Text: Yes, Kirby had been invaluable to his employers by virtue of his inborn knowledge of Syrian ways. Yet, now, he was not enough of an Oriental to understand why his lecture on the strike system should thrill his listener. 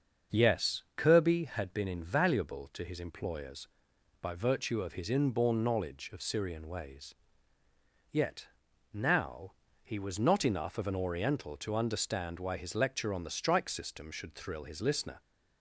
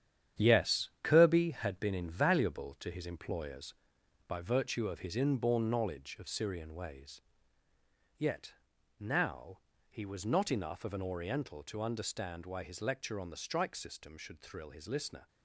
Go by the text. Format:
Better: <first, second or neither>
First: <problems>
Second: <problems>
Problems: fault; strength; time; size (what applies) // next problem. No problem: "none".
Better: first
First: starts louder than the rest; until 1.4 s; 6.5 dB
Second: gets quieter; strong; throughout; 8.5 dB // starts louder than the rest; strong; until 1.5 s; 9.5 dB